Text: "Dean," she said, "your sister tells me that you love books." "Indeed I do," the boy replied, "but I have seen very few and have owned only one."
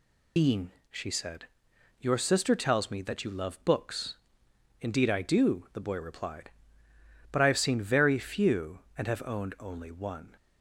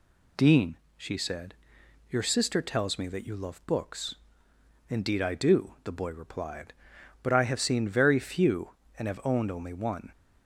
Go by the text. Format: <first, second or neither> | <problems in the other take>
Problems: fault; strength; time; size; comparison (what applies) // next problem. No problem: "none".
second | loses the start of "Dean"; at 0.3 s; 105 ms